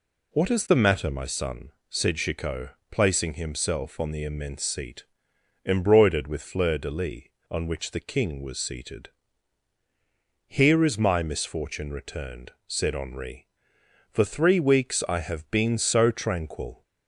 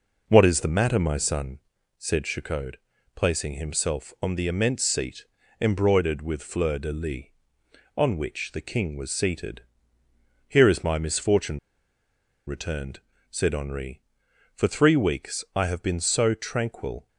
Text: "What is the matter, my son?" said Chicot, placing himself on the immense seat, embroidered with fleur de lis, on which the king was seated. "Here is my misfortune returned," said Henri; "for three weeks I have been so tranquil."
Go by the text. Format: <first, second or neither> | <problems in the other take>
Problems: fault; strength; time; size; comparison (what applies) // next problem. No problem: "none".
first | pauses between "misfortune" and "returned"; noticeable; at 11.5 s; 0.88 s long